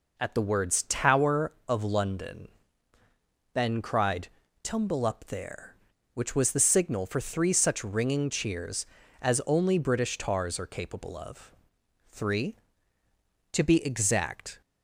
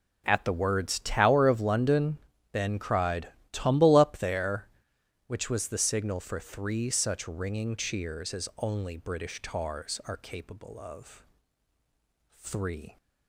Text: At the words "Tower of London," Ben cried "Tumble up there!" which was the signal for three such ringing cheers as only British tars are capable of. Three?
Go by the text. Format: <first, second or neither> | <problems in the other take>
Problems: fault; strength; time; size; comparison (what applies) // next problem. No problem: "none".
second | pauses between "cried" and "Tumble"; slight; at 4.2 s; 0.34 s long; slight in the second // goes on to say "To be exact"; noticeable; from 13.5 s on; 1.1 s long